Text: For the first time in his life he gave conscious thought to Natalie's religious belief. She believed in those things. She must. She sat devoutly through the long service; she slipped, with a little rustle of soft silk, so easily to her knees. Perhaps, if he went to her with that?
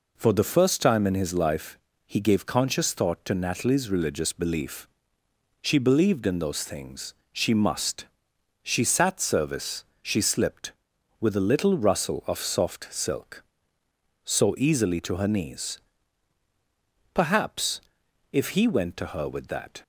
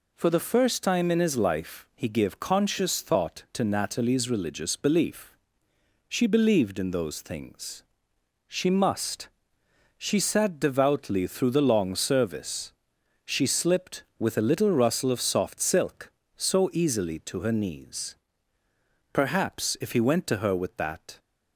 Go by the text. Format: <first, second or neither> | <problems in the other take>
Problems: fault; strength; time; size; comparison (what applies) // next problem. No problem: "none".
second | pauses between "life" and "he"; slight; at 1.7 s; 0.28 s long // skips "devoutly through the long"; at 9.2 s